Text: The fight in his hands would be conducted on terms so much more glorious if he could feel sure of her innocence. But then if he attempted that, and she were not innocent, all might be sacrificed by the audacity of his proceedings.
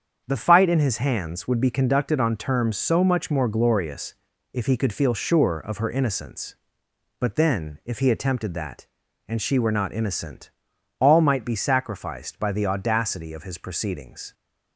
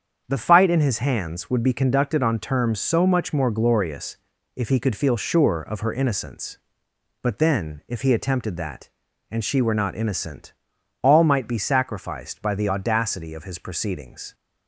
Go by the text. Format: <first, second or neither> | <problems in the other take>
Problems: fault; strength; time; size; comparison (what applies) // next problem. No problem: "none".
neither | starts louder than the rest; strong; the same in both // pauses between "glorious" and "if"; the same in both